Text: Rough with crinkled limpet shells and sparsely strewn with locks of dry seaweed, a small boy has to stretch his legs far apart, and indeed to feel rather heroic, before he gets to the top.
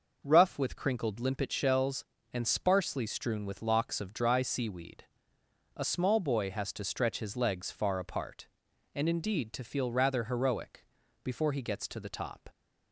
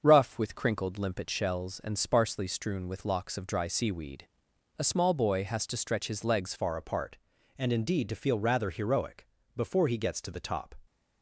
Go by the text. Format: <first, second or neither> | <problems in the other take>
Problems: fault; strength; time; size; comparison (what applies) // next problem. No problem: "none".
first | starts louder than the rest; until 1.0 s; 6.5 dB // changes voice at "far"; from 6.5 s on; 4.2 s long